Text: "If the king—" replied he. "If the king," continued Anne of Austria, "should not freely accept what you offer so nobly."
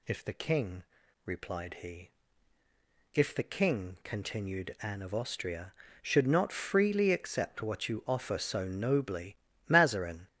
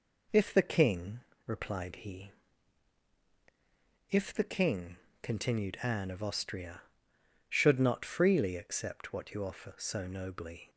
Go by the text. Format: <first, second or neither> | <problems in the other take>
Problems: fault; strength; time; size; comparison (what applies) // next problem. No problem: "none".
second | goes on to say "Mazarin"; from 9.6 s on; 0.58 s long